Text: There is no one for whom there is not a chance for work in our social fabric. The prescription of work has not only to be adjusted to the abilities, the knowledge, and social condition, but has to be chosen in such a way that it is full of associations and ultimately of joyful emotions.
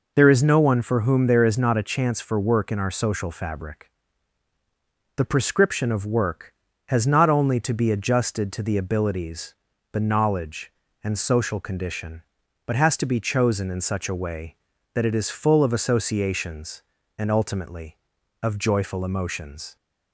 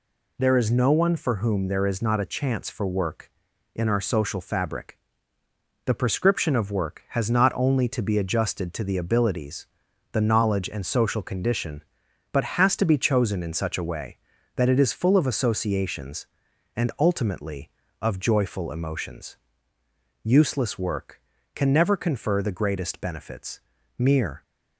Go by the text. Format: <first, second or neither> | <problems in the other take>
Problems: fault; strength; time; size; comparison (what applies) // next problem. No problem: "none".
first | goes on to say "Useless work can never confer the greatest benefits mere"; strong; from 20.2 s on; 4.1 s long